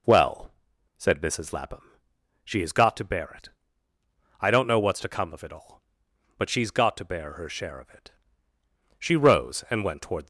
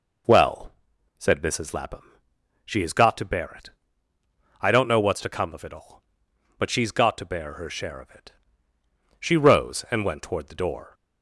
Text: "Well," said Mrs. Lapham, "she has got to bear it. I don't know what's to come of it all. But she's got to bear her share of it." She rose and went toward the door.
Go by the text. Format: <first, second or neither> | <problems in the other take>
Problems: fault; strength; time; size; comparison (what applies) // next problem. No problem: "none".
second | stops before "the door"; at 10.2 s